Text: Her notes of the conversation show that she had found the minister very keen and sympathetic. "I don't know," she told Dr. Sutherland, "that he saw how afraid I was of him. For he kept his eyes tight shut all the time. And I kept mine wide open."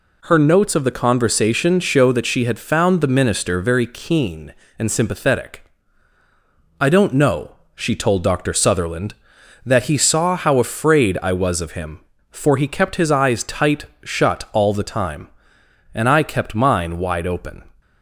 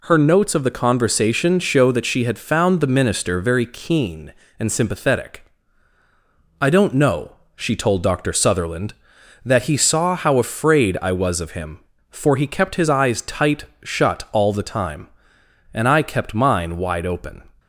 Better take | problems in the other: neither | pauses between "tight" and "shut"; slight; the same in both

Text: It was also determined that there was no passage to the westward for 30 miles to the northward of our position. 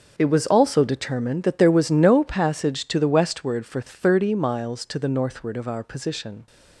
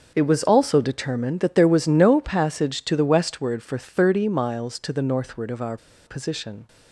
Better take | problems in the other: first | starts louder than the rest; noticeable; until 1.1 s; 6 dB; also in the first // pauses between "our" and "position"; slight; at 5.7 s; 0.29 s long

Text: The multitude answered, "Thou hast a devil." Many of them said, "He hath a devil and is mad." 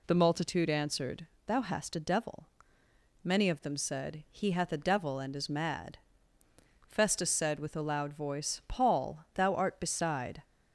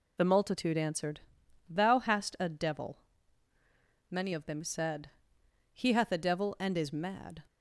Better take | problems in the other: second | goes on to say "Festus said with a loud voice Paul thou art beside"; strong; from 6.8 s on; 3.5 s long

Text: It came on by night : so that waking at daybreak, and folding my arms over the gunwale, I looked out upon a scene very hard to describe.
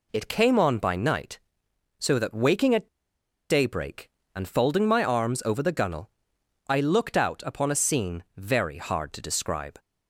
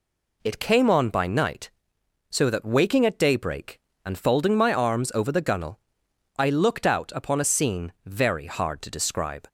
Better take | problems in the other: second | pauses between "at" and "daybreak"; noticeable; at 2.8 s; 0.62 s long

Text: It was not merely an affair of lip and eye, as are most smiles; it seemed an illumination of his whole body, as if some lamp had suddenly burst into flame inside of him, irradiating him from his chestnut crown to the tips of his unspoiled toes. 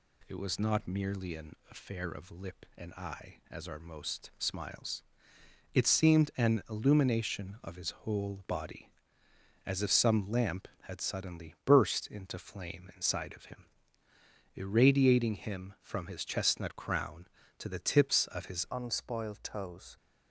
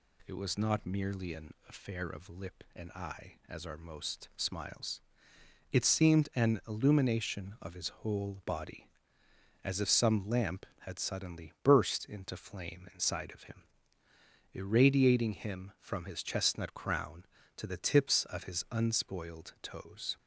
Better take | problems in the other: second | changes voice at "unspoiled"; from 18.7 s on; 1.2 s long

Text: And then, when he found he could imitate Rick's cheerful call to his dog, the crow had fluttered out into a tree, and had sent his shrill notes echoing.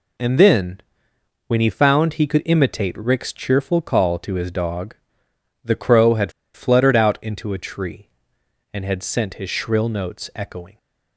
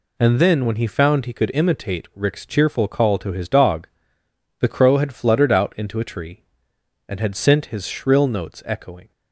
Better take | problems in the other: second | pauses between "had" and "fluttered"; slight; at 6.3 s; 0.23 s long

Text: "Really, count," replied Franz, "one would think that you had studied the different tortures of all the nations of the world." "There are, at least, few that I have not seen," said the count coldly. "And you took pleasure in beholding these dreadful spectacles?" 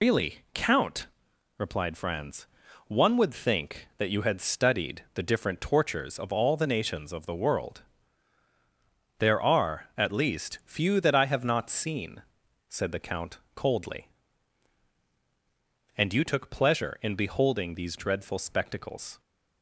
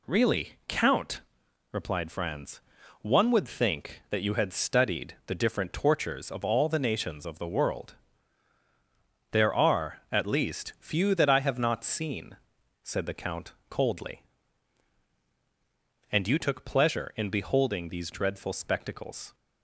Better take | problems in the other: second | loses the start of "Really"; at 0.0 s; 105 ms // pauses between "count" and "coldly"; slight; at 13.3 s; 0.16 s long; slight in the second

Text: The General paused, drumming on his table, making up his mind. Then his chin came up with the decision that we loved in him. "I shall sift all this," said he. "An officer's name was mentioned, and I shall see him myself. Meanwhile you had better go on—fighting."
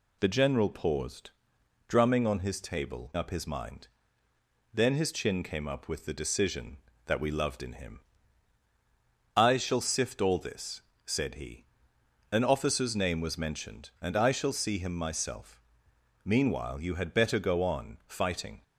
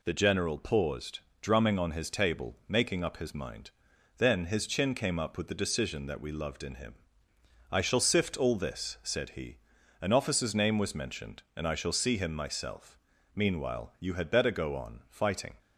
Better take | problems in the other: second | skips "making"; at 3.1 s

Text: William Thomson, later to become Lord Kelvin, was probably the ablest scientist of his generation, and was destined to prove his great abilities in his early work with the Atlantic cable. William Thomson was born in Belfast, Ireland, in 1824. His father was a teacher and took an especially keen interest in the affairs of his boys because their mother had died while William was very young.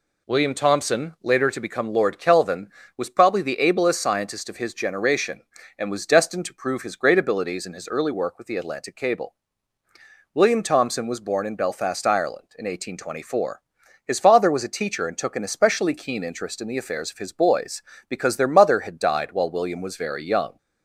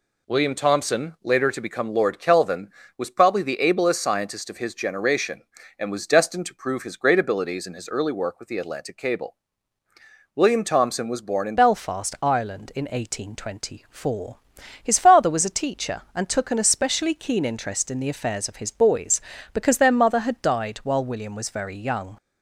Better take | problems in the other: first | changes voice at "Belfast"; from 11.5 s on; 10.6 s long

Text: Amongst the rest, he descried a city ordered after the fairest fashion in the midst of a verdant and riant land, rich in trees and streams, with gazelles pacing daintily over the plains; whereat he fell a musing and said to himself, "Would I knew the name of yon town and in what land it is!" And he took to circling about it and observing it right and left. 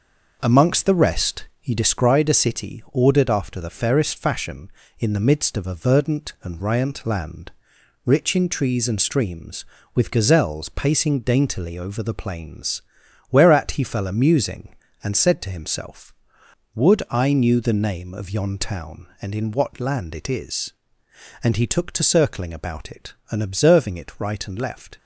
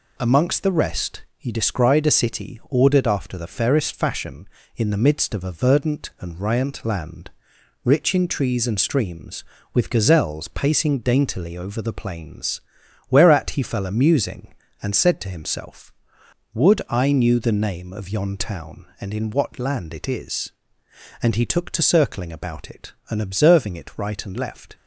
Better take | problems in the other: second | starts louder than the rest; noticeable; until 2.1 s; 6 dB

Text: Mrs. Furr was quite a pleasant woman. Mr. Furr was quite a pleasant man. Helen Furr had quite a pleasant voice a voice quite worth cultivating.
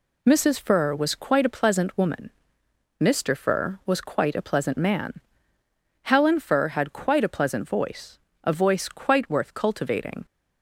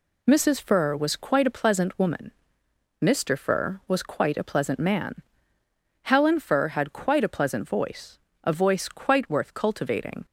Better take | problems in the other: neither | pauses between "voice" and "a"; slight; the same in both

